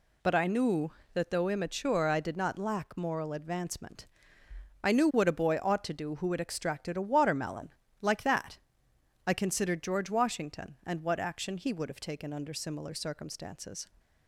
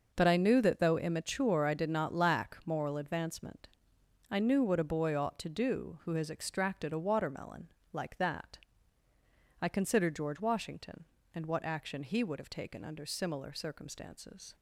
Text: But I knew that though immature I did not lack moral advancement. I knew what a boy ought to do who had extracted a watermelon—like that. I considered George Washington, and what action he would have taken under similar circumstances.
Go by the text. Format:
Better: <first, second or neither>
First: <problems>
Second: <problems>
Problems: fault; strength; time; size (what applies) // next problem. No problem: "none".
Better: first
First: none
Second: says "has" for "had"; at 6.1 s